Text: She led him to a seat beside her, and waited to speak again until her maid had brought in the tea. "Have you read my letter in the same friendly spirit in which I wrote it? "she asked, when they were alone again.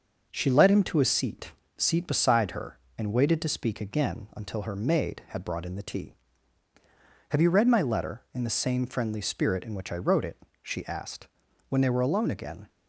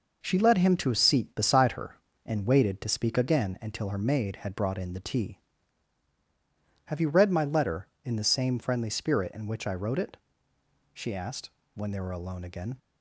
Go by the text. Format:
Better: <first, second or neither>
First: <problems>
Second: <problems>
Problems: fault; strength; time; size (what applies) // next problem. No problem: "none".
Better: second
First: says "seat" twice; at 1.7 s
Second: none